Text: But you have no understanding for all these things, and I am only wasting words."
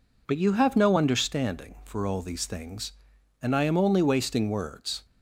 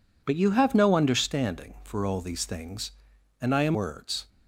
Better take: first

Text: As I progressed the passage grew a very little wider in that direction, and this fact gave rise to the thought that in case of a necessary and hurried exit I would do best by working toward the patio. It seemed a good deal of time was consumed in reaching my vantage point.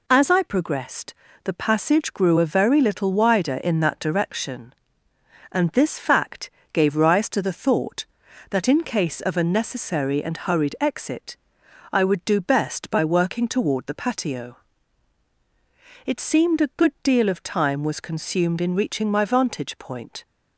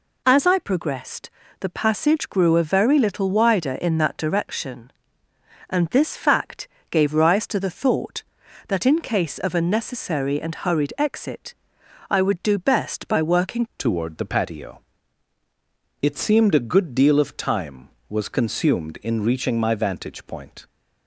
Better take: first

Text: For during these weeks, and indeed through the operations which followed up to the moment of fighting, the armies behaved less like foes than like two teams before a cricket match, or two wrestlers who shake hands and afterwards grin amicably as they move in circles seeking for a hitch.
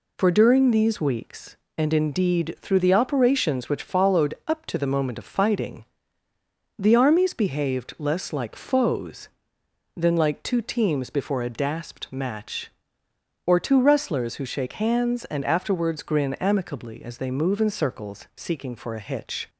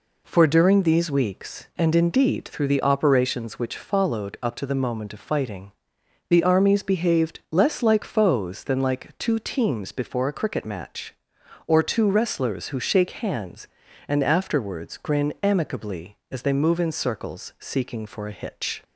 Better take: second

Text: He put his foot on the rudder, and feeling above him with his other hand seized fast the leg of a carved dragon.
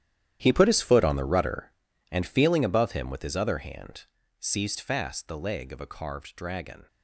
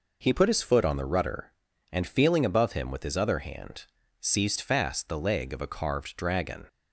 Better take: second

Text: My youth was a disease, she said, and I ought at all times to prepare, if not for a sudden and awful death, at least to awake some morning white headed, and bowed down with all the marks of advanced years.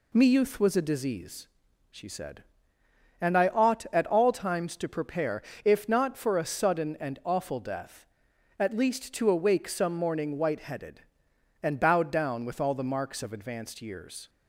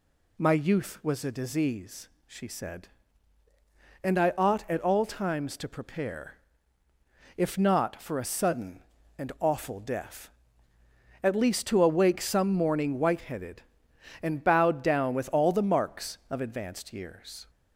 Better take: second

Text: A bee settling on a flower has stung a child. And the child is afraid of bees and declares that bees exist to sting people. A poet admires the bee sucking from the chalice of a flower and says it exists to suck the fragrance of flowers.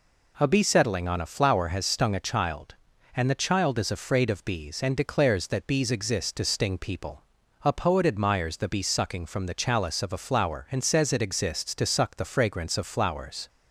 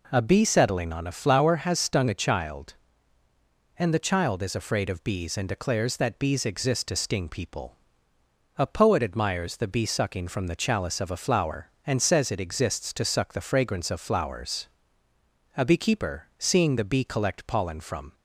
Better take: first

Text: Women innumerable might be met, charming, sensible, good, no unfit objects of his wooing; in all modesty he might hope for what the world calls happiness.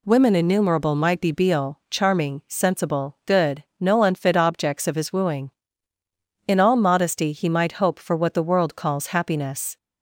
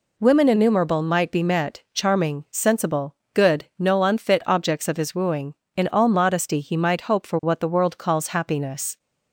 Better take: second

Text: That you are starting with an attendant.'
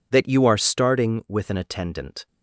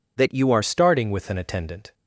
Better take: first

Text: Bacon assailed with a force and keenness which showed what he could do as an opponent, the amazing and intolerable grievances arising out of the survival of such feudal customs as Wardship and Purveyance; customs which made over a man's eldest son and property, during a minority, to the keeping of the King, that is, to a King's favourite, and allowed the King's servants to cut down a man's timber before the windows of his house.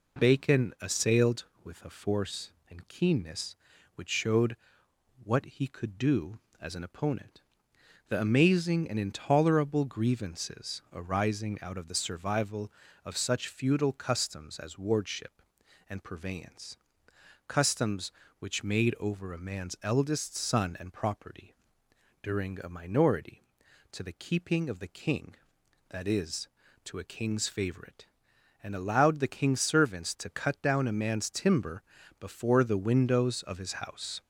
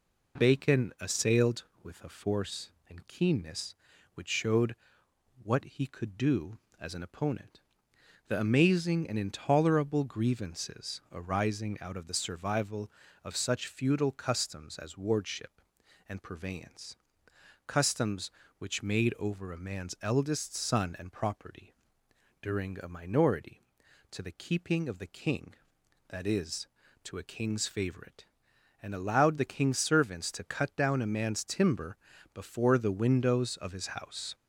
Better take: neither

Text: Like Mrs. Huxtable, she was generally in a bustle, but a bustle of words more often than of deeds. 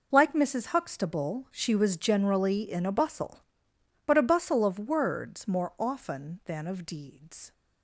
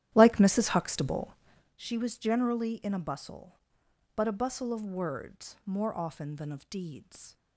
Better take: first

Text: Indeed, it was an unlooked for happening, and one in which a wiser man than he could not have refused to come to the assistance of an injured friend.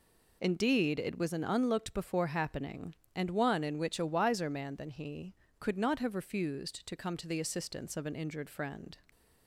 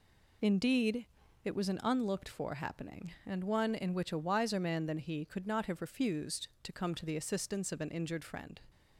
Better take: second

